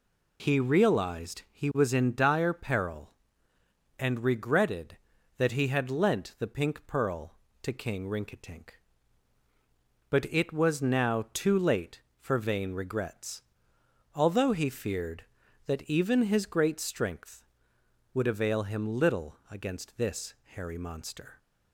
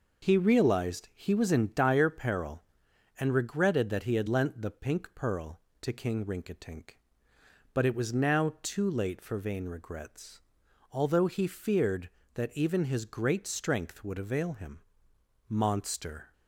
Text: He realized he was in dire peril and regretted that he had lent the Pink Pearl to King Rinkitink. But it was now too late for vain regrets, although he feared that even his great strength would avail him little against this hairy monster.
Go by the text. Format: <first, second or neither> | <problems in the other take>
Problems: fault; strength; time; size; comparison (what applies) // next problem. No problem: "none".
first | skips "little against this hairy"; at 15.1 s